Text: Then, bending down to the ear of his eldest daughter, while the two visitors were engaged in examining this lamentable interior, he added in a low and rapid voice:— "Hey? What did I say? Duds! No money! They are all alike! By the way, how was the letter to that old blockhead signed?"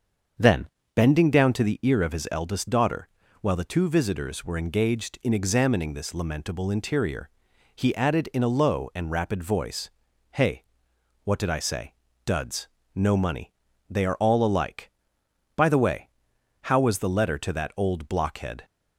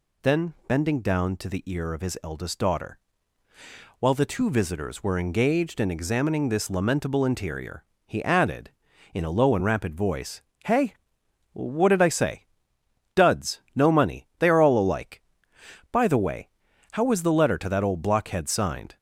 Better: second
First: starts louder than the rest; until 1.6 s; 7 dB // stops before "signed"; at 18.6 s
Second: none

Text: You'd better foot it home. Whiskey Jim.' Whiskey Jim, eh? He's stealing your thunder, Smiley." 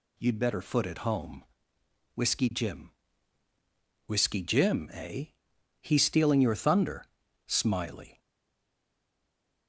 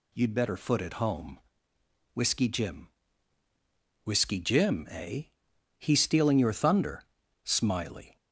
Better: second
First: stays silent after the last word; noticeable; from 8.1 s on; 1.5 s long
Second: none

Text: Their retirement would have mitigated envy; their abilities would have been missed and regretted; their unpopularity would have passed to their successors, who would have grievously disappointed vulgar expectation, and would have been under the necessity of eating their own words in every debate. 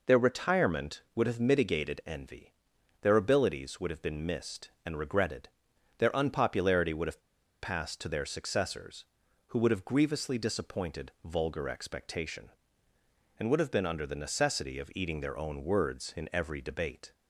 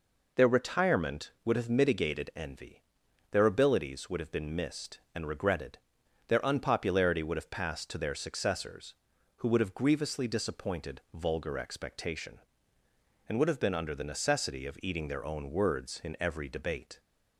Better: second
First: pauses between "have" and "passed"; at 7.2 s; 0.40 s long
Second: none

